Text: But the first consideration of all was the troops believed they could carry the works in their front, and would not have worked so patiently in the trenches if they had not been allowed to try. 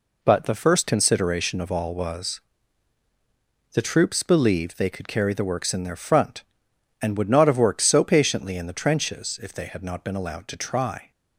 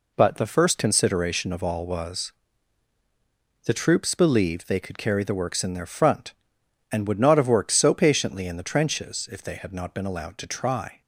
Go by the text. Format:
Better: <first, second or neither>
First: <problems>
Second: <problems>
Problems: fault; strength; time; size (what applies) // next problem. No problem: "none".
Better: neither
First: pauses between "was" and "the"; strong; at 2.3 s; 1.3 s long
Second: pauses between "was" and "the"; strong; at 2.3 s; 1.3 s long